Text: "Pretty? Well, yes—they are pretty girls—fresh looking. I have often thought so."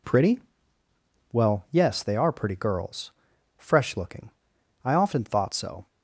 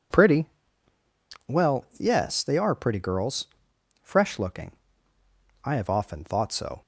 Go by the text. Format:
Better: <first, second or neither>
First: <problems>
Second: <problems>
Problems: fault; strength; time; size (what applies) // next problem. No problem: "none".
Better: second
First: skips "have"; at 4.9 s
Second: none